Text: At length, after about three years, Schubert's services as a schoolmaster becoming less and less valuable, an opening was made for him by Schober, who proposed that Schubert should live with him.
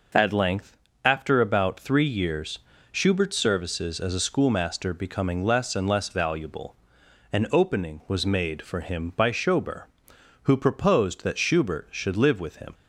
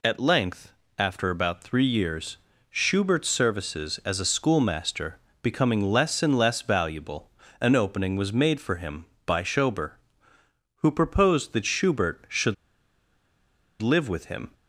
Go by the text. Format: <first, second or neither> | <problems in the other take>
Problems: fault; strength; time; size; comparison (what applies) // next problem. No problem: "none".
first | pauses between "schoolmaster" and "becoming"; slight; at 5.1 s; 0.24 s long // pauses between "should" and "live"; strong; at 12.5 s; 1.2 s long